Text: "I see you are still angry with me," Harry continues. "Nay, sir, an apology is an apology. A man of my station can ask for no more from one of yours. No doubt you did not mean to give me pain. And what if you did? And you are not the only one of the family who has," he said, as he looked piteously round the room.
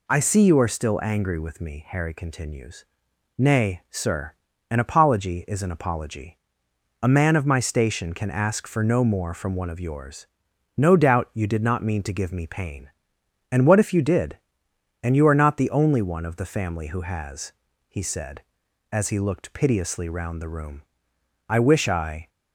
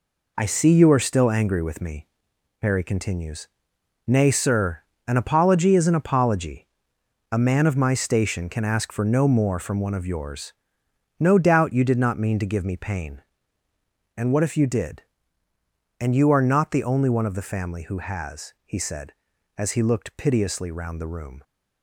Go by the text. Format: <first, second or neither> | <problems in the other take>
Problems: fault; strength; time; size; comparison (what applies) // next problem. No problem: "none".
second | goes on to say "I wish I"; noticeable; from 21.4 s on; 0.80 s long